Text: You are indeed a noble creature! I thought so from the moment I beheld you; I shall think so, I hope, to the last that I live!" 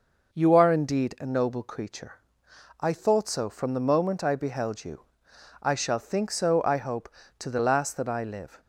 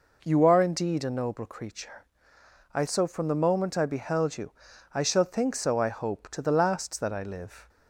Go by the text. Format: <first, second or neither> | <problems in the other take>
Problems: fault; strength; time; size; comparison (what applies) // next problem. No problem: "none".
first | skips "thought"; at 2.8 s